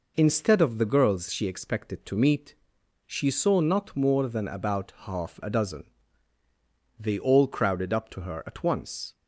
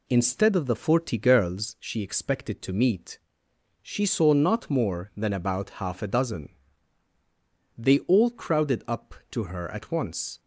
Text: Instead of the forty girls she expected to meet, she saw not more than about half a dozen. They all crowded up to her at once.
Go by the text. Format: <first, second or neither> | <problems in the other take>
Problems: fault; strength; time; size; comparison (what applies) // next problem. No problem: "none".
second | skips "forty"; at 0.8 s